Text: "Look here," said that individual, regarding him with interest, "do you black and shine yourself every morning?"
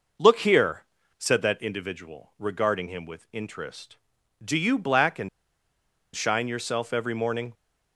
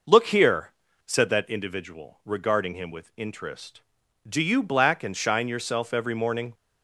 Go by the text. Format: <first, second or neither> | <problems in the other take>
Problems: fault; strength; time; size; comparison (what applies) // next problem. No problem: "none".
second | pauses between "and" and "shine"; noticeable; at 5.2 s; 0.86 s long